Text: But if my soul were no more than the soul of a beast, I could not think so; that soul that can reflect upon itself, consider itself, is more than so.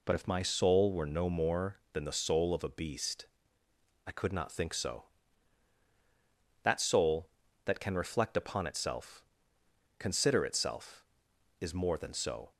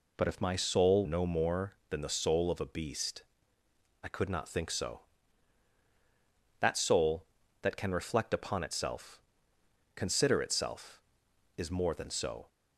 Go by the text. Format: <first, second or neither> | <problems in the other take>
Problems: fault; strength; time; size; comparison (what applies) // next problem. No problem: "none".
first | skips "were"; at 1.0 s